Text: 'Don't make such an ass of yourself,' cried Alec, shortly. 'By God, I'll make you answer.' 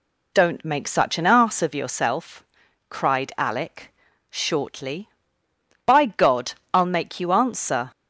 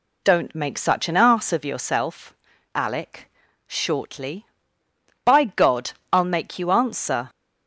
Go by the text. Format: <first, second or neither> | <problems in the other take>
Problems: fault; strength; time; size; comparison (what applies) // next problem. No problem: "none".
first | skips "cried"; at 2.5 s